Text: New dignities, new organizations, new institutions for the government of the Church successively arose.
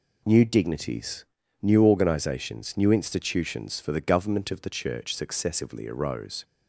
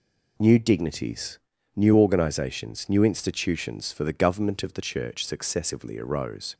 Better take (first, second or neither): neither